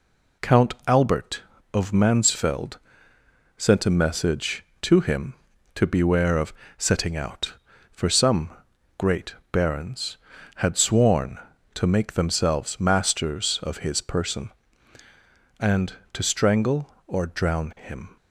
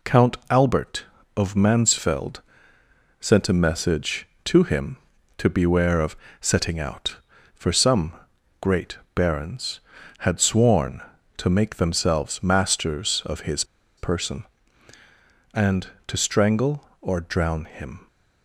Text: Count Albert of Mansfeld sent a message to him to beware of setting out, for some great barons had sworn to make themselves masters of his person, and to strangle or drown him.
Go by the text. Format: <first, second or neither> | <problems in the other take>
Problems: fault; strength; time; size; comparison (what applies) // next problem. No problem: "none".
first | pauses between "Mansfeld" and "sent"; noticeable; at 2.4 s; 0.78 s long; noticeable in the first // pauses between "of" and "setting"; slight; at 6.1 s; 0.26 s long; slight in the first // pauses between "some" and "great"; noticeable; at 8.1 s; 0.48 s long; noticeable in the first // pauses between "great" and "barons"; slight; at 8.9 s; 0.16 s long; slight in the first // pauses between "his" and "person"; slight; at 13.6 s; 0.34 s long